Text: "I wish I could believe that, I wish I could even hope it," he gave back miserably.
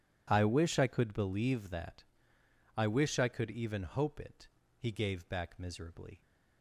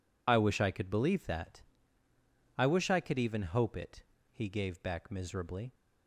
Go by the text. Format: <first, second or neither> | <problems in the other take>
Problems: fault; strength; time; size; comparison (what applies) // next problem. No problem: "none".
first | loses the start of "I"; at 0.2 s; 40 ms